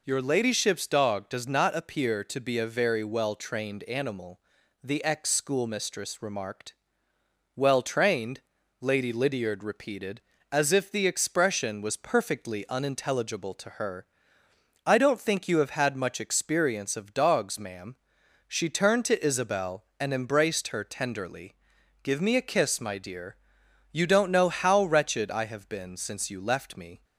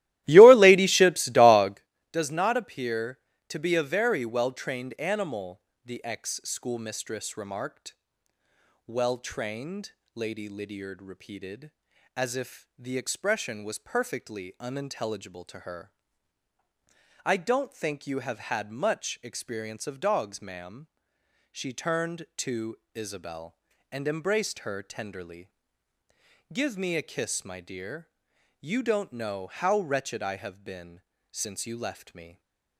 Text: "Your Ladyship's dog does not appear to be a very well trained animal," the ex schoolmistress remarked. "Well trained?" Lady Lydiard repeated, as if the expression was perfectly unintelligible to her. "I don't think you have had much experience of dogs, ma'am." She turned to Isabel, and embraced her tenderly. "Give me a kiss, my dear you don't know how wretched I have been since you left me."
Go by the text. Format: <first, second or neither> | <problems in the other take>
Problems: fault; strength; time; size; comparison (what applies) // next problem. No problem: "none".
first | starts louder than the rest; strong; until 1.8 s; 16 dB // pauses between "to" and "Isabel"; slight; at 22.7 s; 0.16 s long // pauses between "dear" and "you"; noticeable; at 28.0 s; 0.52 s long; noticeable in the first // pauses between "been" and "since"; slight; at 31.0 s; 0.28 s long // stays silent after the last word; slight; from 32.2 s on; 0.5 s long